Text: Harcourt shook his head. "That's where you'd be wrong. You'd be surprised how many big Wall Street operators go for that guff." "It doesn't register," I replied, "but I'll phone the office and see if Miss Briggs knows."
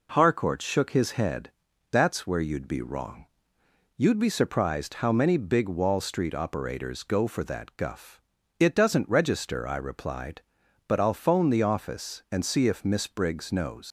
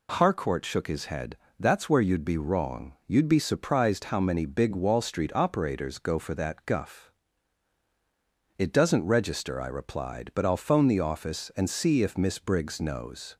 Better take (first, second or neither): second